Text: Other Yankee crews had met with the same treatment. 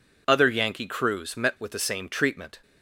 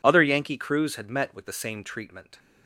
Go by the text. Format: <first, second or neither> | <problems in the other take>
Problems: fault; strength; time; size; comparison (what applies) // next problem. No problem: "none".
second | skips "had"; at 1.3 s